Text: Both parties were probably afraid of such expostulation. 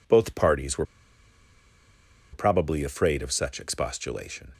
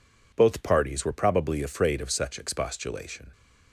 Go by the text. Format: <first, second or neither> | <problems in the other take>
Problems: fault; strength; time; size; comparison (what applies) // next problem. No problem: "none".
second | pauses between "were" and "probably"; strong; at 0.8 s; 1.4 s long